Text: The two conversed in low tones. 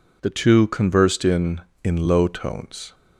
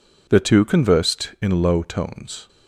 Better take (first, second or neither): second